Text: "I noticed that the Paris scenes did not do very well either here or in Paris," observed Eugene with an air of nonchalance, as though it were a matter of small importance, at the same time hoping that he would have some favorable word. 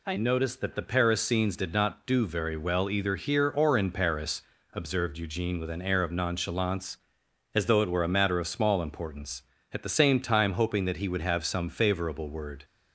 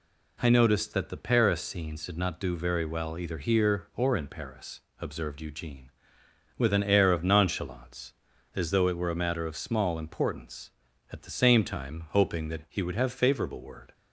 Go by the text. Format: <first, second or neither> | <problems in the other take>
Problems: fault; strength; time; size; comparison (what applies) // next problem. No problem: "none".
first | skips "some"; at 13.1 s